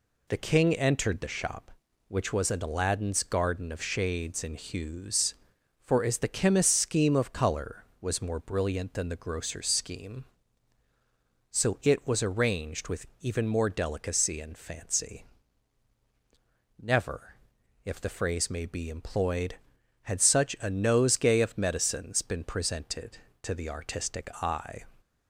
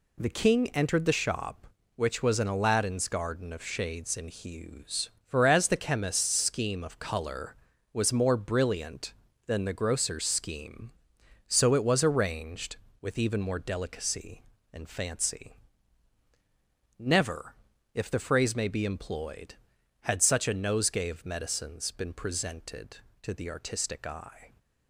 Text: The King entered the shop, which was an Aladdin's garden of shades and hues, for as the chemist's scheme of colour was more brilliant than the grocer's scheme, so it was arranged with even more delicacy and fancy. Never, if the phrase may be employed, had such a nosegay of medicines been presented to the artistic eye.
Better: neither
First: none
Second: none

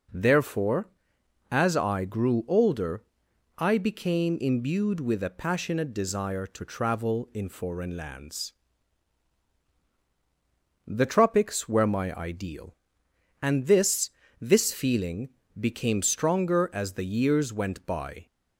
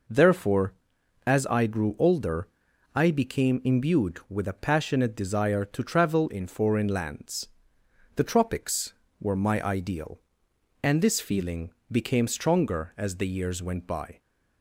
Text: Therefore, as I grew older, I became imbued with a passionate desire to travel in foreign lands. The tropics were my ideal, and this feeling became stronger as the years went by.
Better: second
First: says "this" twice; at 14.3 s // pauses between "feeling" and "became"; slight; at 15.2 s; 0.30 s long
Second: pauses between "feeling" and "became"; slight; at 11.7 s; 0.20 s long

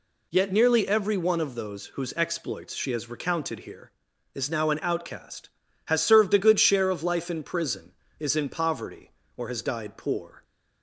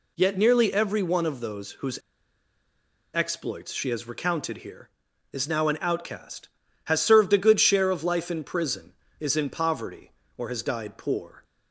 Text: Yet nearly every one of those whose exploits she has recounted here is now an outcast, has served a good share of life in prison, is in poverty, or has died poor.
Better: first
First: none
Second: pauses between "whose" and "exploits"; at 1.9 s; 1.1 s long

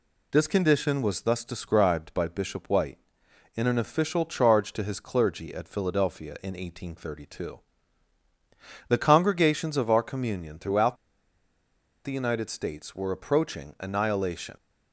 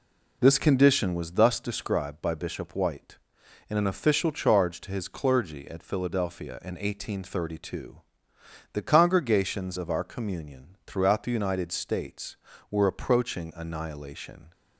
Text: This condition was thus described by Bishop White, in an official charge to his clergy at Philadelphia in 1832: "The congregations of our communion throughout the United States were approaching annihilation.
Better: second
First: pauses between "throughout" and "the"; at 10.9 s; 1.0 s long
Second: none

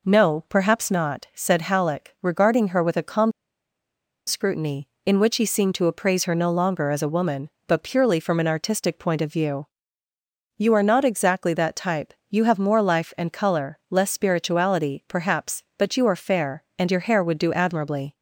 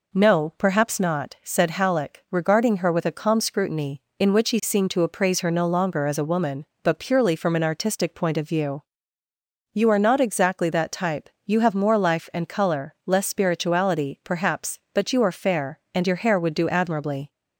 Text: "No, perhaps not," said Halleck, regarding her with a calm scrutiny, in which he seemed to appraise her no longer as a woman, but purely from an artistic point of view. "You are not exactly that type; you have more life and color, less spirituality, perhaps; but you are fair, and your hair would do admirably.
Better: second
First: pauses between "calm" and "scrutiny"; noticeable; at 3.3 s; 0.96 s long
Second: none

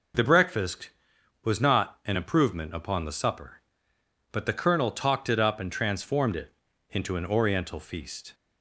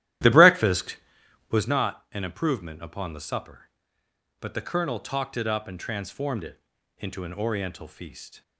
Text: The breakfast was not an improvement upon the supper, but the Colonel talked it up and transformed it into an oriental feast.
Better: first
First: pauses between "it" and "into"; slight; at 6.5 s; 0.36 s long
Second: starts louder than the rest; strong; until 1.7 s; 13 dB // pauses between "it" and "into"; slight; at 6.5 s; 0.36 s long

